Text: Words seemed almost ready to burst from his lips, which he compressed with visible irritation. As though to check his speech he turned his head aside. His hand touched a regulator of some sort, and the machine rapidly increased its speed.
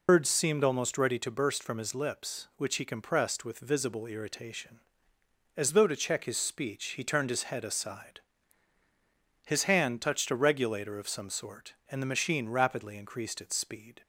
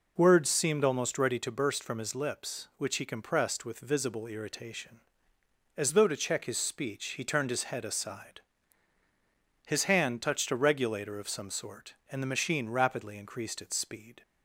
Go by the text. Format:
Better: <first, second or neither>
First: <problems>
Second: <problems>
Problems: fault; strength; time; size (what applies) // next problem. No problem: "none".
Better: second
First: loses the start of "Words"; at 0.0 s; 115 ms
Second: none